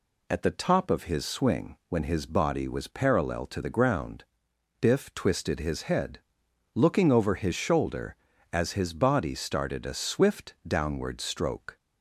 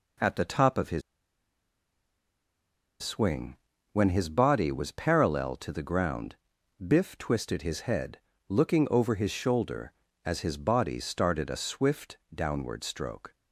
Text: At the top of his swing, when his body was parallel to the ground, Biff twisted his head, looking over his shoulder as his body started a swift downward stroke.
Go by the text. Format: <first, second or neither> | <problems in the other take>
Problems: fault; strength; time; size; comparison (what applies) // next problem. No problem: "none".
first | pauses between "his" and "swing"; strong; at 1.0 s; 2.0 s long // pauses between "swift" and "downward"; slight; at 12.1 s; 0.16 s long